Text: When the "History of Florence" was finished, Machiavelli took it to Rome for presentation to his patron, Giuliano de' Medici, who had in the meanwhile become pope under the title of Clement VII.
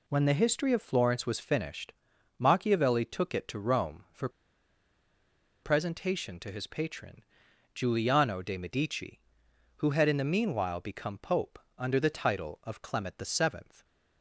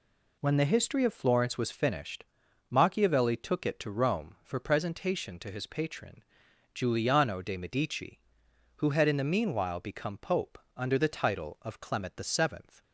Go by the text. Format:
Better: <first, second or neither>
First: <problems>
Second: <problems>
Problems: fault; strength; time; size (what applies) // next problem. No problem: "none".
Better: second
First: pauses between "for" and "presentation"; strong; at 4.2 s; 1.3 s long // pauses between "pope" and "under"; slight; at 11.5 s; 0.18 s long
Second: pauses between "pope" and "under"; slight; at 10.5 s; 0.16 s long